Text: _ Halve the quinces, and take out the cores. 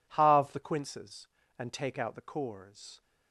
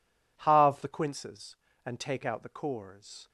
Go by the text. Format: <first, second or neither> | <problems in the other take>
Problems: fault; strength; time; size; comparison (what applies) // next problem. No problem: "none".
neither | none